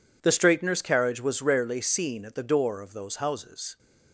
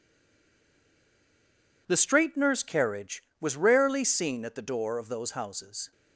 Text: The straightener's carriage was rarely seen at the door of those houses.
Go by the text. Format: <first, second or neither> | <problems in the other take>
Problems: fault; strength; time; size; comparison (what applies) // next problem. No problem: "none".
first | stays silent before the first word; noticeable; until 1.8 s; 1.8 s long